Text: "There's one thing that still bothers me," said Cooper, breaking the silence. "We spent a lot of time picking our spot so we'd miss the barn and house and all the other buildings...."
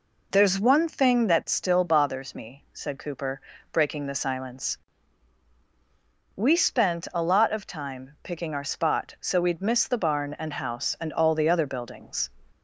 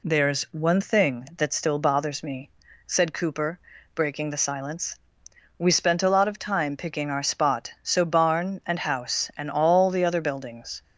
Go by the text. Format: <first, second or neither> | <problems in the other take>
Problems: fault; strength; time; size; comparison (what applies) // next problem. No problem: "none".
first | skips "we'd miss the"; at 8.0 s